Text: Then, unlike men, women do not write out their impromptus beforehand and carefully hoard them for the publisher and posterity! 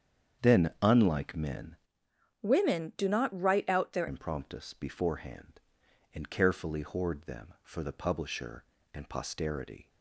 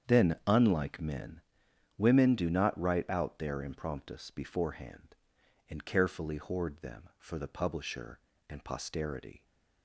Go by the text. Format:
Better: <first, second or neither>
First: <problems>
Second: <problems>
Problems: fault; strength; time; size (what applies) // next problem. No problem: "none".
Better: second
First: starts louder than the rest; strong; until 1.5 s; 8 dB // changes voice from "women" to "their"; from 2.4 to 4.0 s; 1.6 s long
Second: starts louder than the rest; strong; until 1.1 s; 8 dB